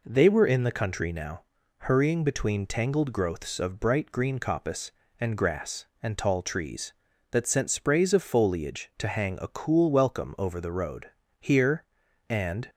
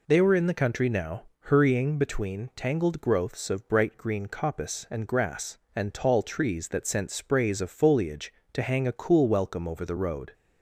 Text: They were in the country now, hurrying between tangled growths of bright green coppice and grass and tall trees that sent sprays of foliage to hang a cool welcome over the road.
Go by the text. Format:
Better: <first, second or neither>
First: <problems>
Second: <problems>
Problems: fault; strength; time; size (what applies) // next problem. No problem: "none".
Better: second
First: goes on to say "Here and"; noticeable; from 11.3 s on; 1.3 s long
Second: none